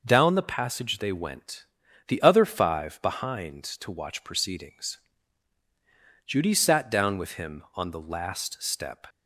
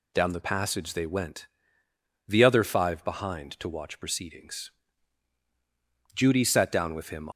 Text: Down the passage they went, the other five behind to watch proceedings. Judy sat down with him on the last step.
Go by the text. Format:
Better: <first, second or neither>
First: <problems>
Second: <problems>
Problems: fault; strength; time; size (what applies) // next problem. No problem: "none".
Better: first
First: none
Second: stops before "on the last step"; at 7.3 s